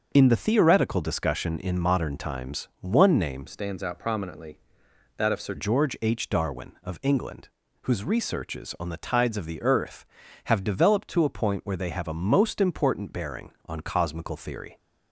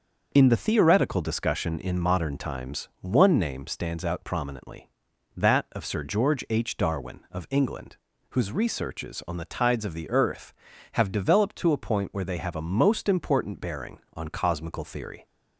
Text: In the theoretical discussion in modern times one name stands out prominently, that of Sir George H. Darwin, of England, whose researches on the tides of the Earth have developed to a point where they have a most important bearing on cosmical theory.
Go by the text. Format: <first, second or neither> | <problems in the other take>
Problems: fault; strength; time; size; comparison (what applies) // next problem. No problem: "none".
second | starts louder than the rest; until 1.1 s; 6.5 dB; also in the second // changes voice from "stands" to "Sir"; from 3.4 to 5.5 s; 2.1 s long